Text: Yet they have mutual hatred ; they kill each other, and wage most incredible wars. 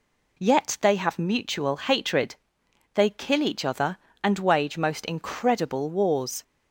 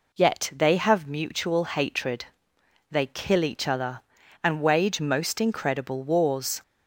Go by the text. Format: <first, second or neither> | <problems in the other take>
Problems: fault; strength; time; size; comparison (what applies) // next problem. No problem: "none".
neither | none